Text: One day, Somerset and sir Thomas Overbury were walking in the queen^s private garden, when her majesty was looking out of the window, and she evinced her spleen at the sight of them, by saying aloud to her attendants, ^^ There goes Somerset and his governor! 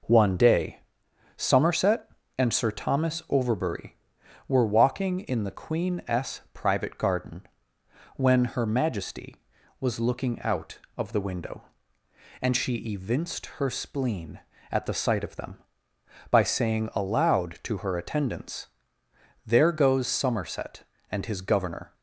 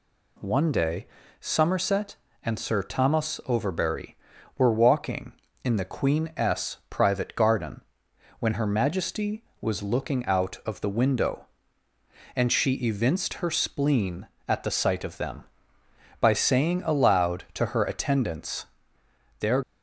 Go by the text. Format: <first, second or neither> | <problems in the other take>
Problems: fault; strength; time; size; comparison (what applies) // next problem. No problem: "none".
first | stops before "goes Somerset and his governor"; at 19.6 s